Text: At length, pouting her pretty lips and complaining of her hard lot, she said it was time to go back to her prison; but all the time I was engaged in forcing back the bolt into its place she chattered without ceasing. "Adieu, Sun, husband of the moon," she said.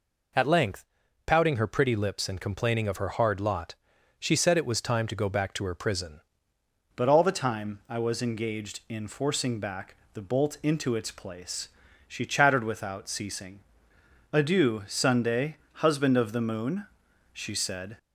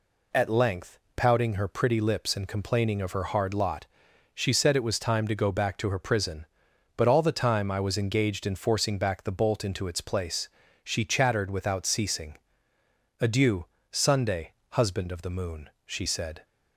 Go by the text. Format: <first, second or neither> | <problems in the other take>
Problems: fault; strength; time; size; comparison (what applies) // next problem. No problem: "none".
second | changes voice at "but"; from 6.9 s on; 11.0 s long // pauses between "back" and "the"; slight; at 9.9 s; 0.18 s long // pauses between "place" and "she"; slight; at 11.6 s; 0.36 s long; slight in the second